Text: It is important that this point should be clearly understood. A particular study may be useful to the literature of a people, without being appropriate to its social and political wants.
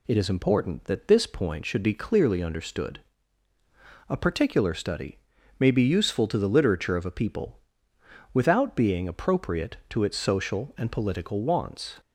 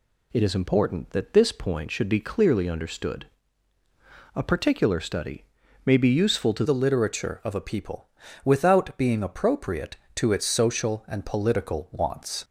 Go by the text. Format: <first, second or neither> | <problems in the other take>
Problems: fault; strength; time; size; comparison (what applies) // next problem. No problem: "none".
first | pauses between "study" and "may"; at 5.4 s; 0.40 s long; also in the first // changes voice at "the"; from 6.6 s on; 5.8 s long